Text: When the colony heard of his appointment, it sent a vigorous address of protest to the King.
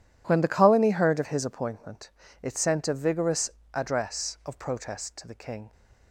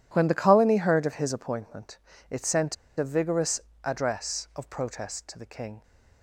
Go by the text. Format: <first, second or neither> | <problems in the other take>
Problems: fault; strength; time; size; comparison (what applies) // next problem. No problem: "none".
first | pauses between "sent" and "a"; slight; at 2.7 s; 0.23 s long // pauses between "vigorous" and "address"; slight; at 3.6 s; 0.24 s long; slight in the first